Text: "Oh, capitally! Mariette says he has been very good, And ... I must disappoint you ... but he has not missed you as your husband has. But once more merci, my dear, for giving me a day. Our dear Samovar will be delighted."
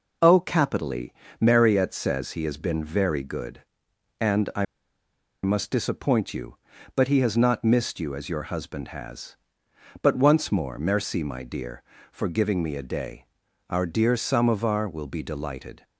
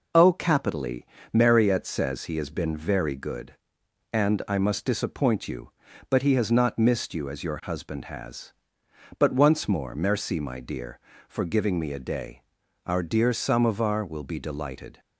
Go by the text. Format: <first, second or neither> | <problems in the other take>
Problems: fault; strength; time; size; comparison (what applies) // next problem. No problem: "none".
second | pauses between "I" and "must"; noticeable; at 4.6 s; 0.78 s long